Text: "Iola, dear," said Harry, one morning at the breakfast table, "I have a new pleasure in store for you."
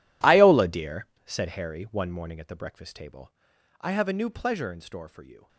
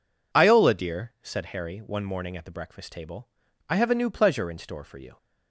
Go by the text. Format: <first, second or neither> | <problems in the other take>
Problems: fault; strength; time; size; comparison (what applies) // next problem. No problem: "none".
second | gets quieter; strong; throughout; 17.5 dB